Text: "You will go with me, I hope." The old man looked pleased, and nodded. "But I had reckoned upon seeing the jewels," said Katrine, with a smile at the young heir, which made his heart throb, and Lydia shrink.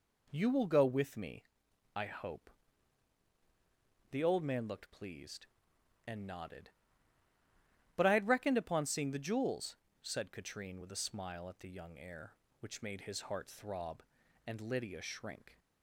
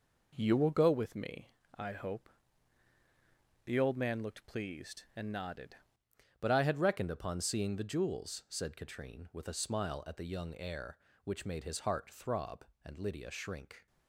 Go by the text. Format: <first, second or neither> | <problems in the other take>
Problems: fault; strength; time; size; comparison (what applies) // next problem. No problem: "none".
first | changes voice at "But"; from 6.3 s on; 7.5 s long